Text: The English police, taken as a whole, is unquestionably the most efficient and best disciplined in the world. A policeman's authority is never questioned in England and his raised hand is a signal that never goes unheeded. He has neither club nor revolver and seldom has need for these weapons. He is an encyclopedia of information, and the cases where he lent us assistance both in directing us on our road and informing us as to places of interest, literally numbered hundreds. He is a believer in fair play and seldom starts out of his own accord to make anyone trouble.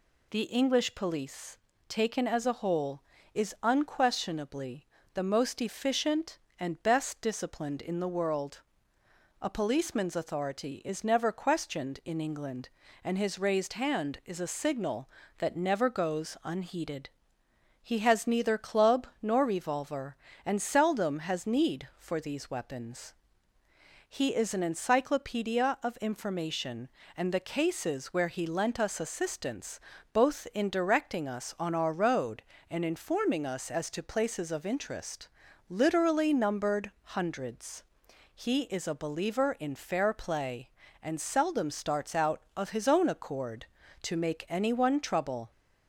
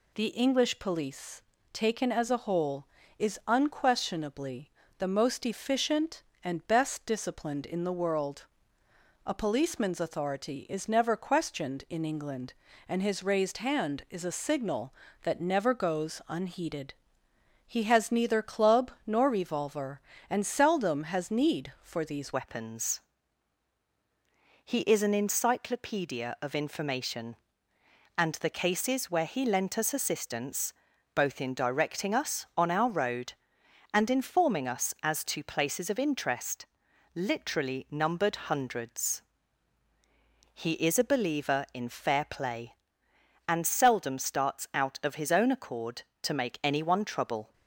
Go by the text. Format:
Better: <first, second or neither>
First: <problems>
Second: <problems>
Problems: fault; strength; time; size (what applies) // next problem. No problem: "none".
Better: first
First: pauses between "unquestionably" and "the"; slight; at 4.8 s; 0.30 s long // pauses between "club" and "nor"; slight; at 19.0 s; 0.16 s long // pauses between "assistance" and "both"; slight; at 29.7 s; 0.34 s long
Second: pauses between "unquestionably" and "the"; slight; at 4.6 s; 0.30 s long // pauses between "club" and "nor"; slight; at 18.9 s; 0.16 s long // changes voice at "weapons"; from 22.3 s on; 25.2 s long // pauses between "assistance" and "both"; at 30.7 s; 0.42 s long